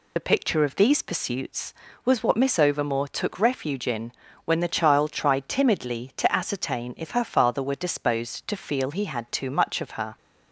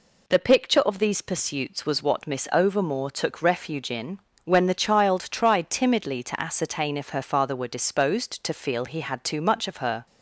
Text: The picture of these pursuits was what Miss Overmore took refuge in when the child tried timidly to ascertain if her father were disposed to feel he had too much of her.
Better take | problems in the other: second | loses the start of "The"; at 0.1 s; 30 ms // pauses between "in" and "when"; slight; at 4.1 s; 0.32 s long; slight in the second

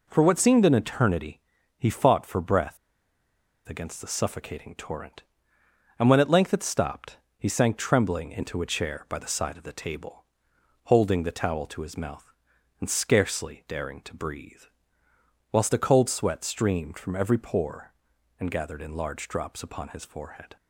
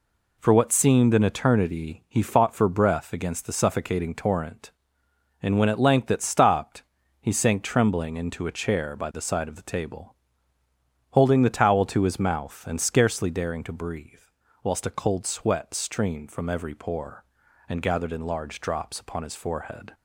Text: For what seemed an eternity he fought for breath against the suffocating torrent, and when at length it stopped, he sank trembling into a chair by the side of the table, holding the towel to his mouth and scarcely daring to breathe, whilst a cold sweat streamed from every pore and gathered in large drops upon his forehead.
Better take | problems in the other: second | pauses between "eternity" and "he"; at 1.3 s; 0.38 s long // pauses between "breath" and "against"; noticeable; at 2.7 s; 0.90 s long

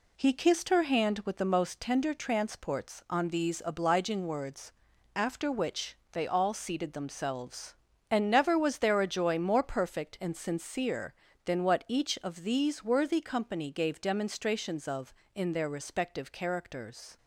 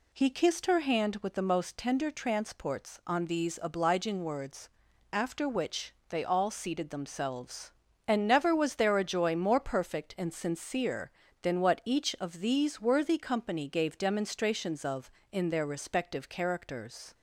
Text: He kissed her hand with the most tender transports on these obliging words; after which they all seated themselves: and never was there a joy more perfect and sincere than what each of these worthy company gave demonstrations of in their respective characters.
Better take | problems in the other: second | gets quieter; noticeable; throughout; 5 dB // pauses between "which" and "they"; slight; at 5.9 s; 0.16 s long; slight in the second

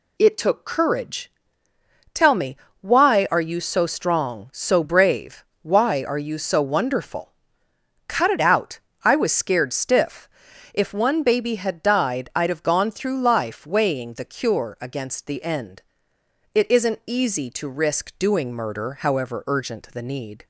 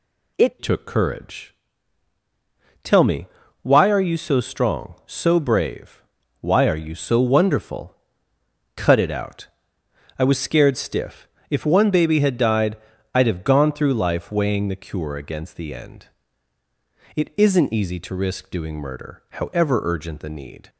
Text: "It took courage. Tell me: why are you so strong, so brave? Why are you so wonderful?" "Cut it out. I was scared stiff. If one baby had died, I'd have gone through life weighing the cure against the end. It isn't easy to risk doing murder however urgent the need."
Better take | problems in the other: first | changes voice at "took"; from 0.6 s on; 20.0 s long

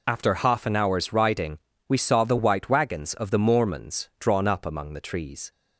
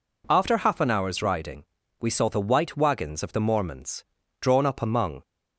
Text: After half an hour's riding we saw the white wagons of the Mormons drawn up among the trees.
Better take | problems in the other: first | pauses between "riding" and "we"; at 1.6 s; 0.38 s long; slight in the first // pauses between "Mormons" and "drawn"; at 4.0 s; 0.38 s long // stops before "the trees"; at 5.2 s

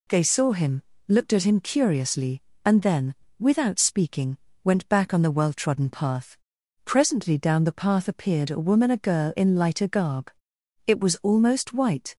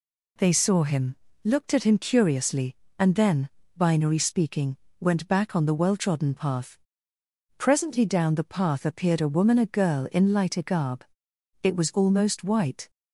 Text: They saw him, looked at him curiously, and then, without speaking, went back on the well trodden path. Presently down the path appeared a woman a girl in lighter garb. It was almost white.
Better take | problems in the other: first | says "binary" for "without"; at 3.7 s

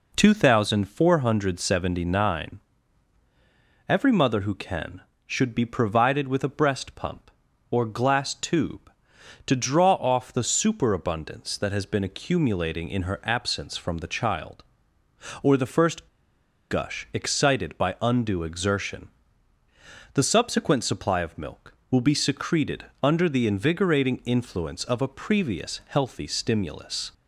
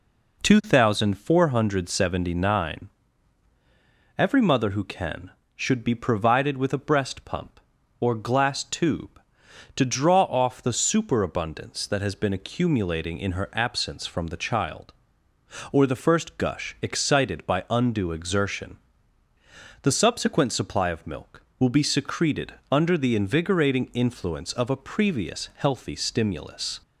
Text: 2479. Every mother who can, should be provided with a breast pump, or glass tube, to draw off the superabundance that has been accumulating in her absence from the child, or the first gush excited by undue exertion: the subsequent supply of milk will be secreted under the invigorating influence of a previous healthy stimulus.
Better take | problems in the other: second | pauses between "first" and "gush"; noticeable; at 16.0 s; 0.63 s long // pauses between "secreted" and "under"; slight; at 22.8 s; 0.16 s long; slight in the second

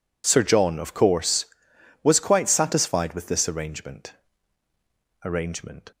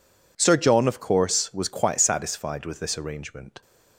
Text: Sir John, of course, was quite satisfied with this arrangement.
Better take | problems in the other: second | says "arrangement" twice; at 5.2 s

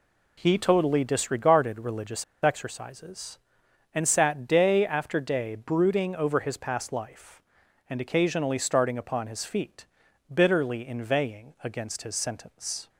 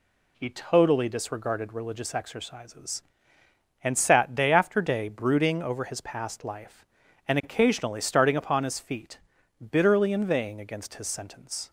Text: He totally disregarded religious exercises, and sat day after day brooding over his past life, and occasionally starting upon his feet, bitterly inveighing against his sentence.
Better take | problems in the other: second | pauses between "religious" and "exercises"; slight; at 2.2 s; 0.18 s long

